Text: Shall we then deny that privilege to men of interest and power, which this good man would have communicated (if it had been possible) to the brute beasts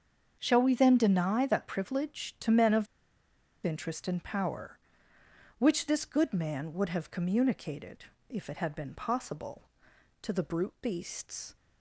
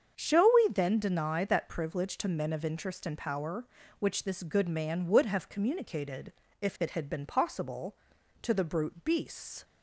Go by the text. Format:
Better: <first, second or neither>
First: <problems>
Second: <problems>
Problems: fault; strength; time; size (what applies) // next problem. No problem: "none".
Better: second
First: starts louder than the rest; until 1.4 s; 7 dB // pauses between "of" and "interest"; noticeable; at 2.8 s; 0.78 s long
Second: starts louder than the rest; until 1.2 s; 7 dB